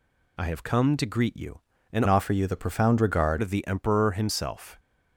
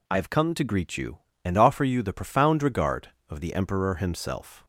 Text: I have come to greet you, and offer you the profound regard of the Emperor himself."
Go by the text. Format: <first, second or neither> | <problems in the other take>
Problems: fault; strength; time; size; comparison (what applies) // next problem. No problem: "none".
second | changes voice from "offer" to "regard"; from 2.0 to 3.3 s; 1.3 s long